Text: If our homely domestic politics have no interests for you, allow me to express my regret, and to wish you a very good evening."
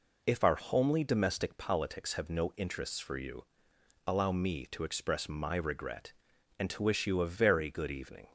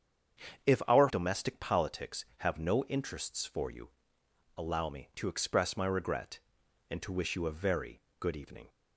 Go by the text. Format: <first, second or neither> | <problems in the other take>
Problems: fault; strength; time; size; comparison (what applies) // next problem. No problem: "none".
first | starts louder than the rest; strong; until 1.7 s; 7.5 dB // skips "homely"; at 1.0 s // pauses between "very" and "good"; slight; at 8.0 s; 0.18 s long